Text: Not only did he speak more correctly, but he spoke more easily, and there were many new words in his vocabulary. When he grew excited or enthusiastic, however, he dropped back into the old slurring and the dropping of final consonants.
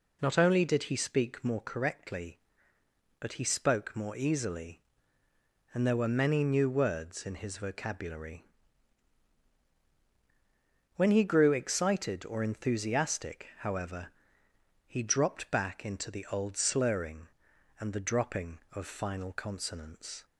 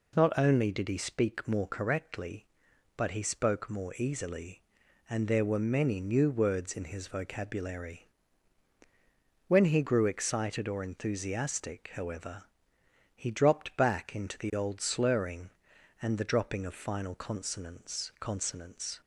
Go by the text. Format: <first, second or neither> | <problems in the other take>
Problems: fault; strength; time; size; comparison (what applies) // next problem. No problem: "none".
first | says "consonants" twice; at 18.2 s